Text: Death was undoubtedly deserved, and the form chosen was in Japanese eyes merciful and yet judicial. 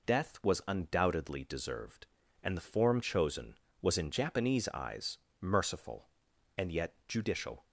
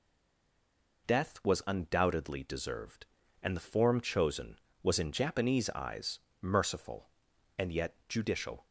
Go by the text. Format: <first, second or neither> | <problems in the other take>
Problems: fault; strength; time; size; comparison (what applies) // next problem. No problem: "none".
first | stays silent before the first word; until 1.0 s; 1.0 s long // pauses between "eyes" and "merciful"; slight; at 6.1 s; 0.23 s long; slight in the first